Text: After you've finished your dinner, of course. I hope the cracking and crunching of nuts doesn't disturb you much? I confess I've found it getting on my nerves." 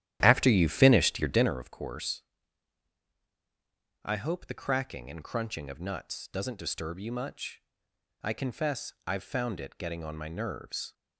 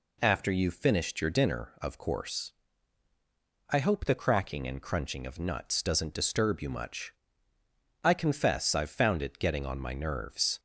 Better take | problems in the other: second | starts louder than the rest; strong; until 1.7 s; 12 dB

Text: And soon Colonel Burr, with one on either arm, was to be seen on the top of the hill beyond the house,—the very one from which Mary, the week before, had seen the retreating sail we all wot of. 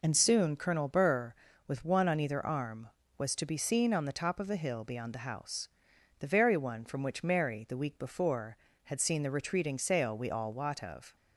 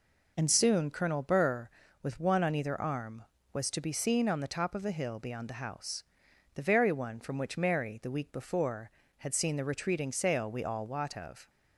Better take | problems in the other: neither | none

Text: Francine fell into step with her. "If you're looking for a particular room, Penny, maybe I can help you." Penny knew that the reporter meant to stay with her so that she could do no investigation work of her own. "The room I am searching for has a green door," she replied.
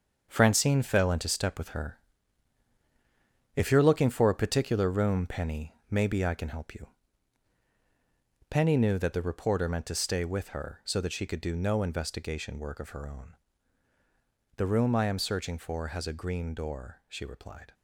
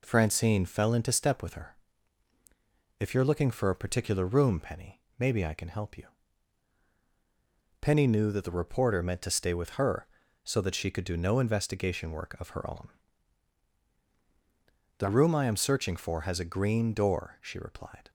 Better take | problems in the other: second | gets quieter; strong; throughout; 8.5 dB

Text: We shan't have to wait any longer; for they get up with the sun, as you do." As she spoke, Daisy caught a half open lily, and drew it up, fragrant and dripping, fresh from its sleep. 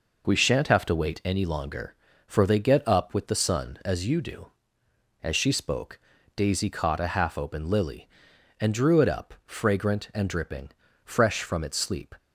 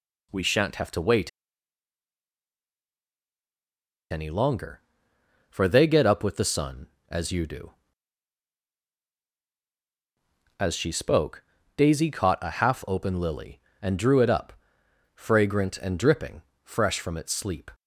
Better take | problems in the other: first | pauses between "wait" and "any"; strong; at 1.2 s; 2.8 s long

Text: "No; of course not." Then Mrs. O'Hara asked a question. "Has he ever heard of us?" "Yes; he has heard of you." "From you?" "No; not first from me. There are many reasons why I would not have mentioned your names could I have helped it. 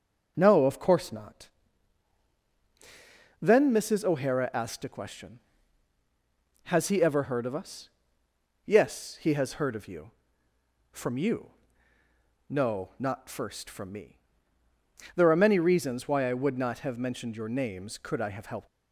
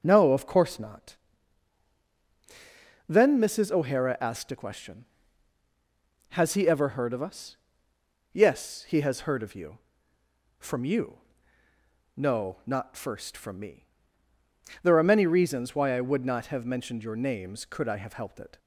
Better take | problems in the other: second | starts louder than the rest; until 1.3 s; 6.5 dB; also in the second // stops before "it"; at 18.6 s

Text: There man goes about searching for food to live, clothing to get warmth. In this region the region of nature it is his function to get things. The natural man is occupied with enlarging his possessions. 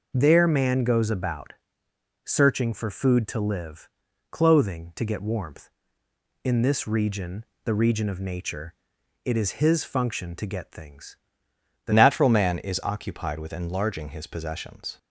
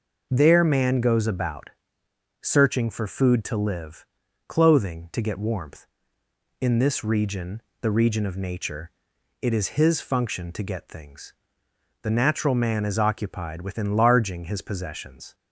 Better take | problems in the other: second | pauses between "about" and "searching"; noticeable; at 1.5 s; 0.72 s long; noticeable in the second // pauses between "region" and "the"; slight; at 7.4 s; 0.20 s long; slight in the second // pauses between "nature" and "it"; noticeable; at 8.7 s; 0.54 s long; noticeable in the second // changes voice at "natural"; from 11.9 s on; 3.0 s long

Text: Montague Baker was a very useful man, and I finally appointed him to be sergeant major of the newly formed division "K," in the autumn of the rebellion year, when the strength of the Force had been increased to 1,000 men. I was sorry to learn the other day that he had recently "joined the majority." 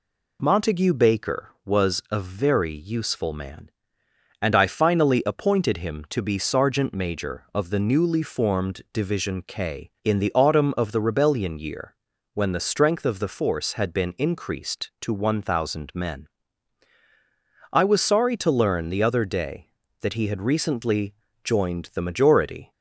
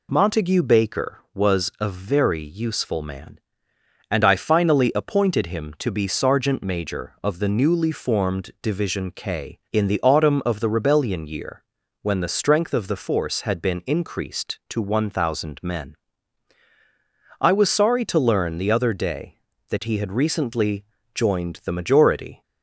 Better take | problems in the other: neither | pauses between "recently" and "joined"; slight; the same in both

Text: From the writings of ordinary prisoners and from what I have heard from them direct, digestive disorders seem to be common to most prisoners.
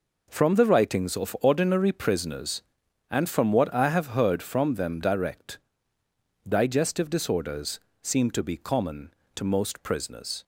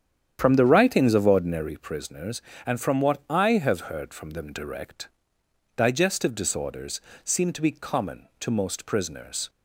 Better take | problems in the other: first | starts louder than the rest; strong; until 1.7 s; 9 dB // pauses between "disorders" and "seem"; slight; at 7.0 s; 0.24 s long; slight in the first

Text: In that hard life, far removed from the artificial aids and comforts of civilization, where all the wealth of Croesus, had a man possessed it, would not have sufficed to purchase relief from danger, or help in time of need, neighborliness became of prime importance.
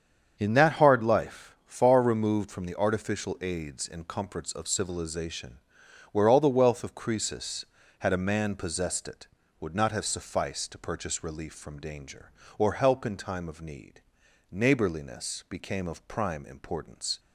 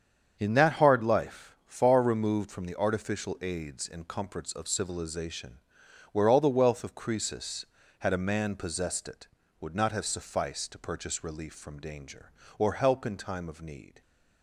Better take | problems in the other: first | starts louder than the rest; strong; until 1.4 s; 7.5 dB; strong in the first // stops before "neighborliness became of prime importance"; at 14.0 s

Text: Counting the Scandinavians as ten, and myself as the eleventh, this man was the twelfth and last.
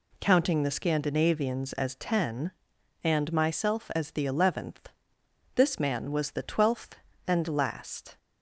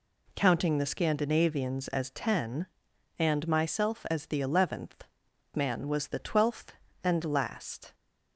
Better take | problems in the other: first | skips "this"; at 5.2 s

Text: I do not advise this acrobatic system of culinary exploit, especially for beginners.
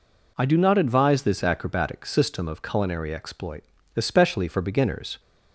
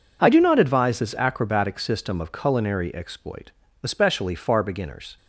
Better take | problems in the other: first | says "far" for "for"; at 4.3 s

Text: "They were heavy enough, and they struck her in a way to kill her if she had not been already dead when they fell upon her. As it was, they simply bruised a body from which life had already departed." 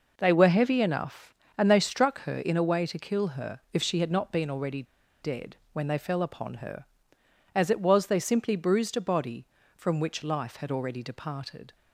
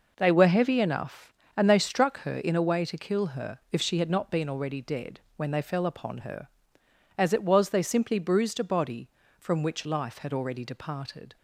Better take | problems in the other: second | pauses between "already" and "dead"; at 4.8 s; 0.38 s long // pauses between "dead" and "when"; slight; at 5.5 s; 0.16 s long; slight in the second

